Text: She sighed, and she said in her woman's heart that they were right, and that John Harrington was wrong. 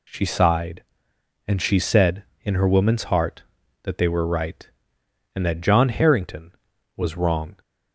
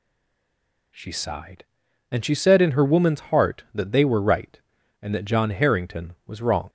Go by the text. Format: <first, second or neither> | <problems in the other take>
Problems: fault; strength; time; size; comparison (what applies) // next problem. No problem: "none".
first | stays silent before the first word; slight; until 0.9 s; 0.9 s long